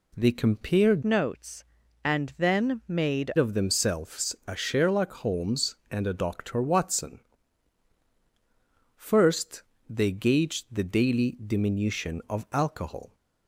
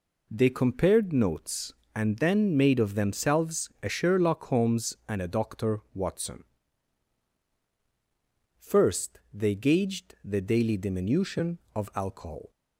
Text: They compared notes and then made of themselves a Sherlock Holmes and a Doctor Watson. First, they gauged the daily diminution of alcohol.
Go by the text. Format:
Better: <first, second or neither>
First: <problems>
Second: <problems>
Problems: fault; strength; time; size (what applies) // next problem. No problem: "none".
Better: second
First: changes voice from "notes" to "made"; from 1.0 to 3.2 s; 2.2 s long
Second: none